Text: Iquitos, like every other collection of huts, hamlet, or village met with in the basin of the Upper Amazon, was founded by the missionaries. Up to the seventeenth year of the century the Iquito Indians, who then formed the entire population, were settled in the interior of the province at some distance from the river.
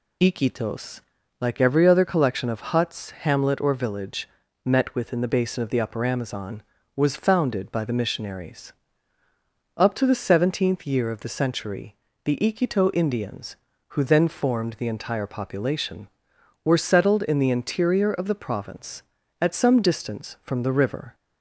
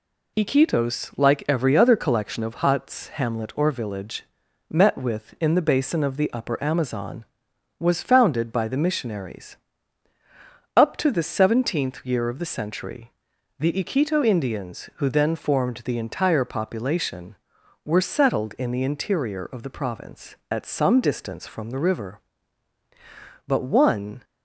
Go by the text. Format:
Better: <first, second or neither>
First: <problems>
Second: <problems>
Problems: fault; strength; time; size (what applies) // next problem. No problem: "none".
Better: first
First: pauses between "village" and "met"; slight; at 4.2 s; 0.36 s long // pauses between "century" and "the"; slight; at 11.9 s; 0.26 s long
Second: pauses between "village" and "met"; at 4.2 s; 0.44 s long // pauses between "century" and "the"; noticeable; at 13.1 s; 0.48 s long // goes on to say "But one"; noticeable; from 23.4 s on; 0.78 s long